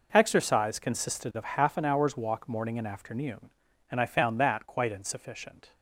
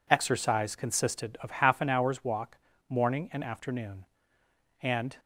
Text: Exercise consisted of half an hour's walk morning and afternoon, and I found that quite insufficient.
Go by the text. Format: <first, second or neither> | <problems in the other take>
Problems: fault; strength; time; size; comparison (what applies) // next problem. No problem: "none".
first | pauses between "walk" and "morning"; slight; at 2.5 s; 0.32 s long // stops before "I found that quite insufficient"; at 5.1 s